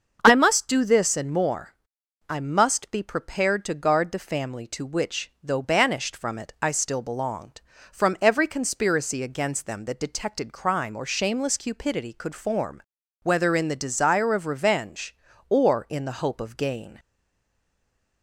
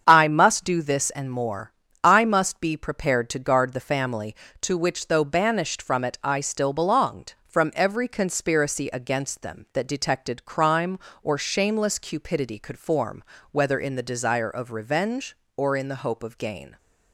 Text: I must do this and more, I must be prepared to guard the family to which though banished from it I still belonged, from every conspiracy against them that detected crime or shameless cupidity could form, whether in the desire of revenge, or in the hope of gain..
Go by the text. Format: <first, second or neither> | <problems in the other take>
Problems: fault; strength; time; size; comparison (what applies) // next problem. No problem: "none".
second | starts louder than the rest; until 1.2 s; 6.5 dB; strong in the second // stays silent after the last word; noticeable; from 16.9 s on; 1.3 s long